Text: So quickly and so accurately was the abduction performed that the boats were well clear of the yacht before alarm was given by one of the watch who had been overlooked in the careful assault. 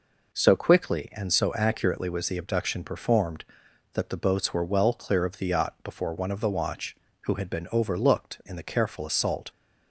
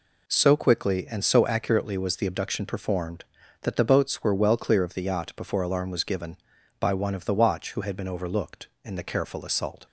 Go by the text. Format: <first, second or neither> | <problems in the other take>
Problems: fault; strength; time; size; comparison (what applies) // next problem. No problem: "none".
second | skips "alarm was given by"; at 6.1 s